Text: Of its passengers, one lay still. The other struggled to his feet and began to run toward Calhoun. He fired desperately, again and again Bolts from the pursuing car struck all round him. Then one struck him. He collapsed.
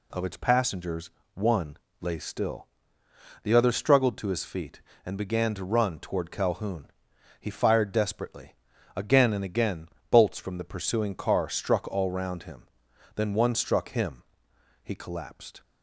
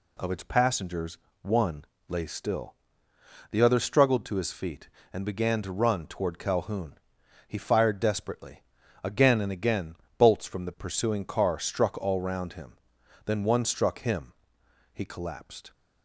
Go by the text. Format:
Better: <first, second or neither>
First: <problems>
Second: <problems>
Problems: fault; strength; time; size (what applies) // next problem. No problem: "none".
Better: neither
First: pauses between "one" and "lay"; slight; at 1.7 s; 0.24 s long // pauses between "again" and "Bolts"; slight; at 9.8 s; 0.22 s long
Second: pauses between "one" and "lay"; slight; at 1.8 s; 0.24 s long // pauses between "again" and "Bolts"; slight; at 9.9 s; 0.22 s long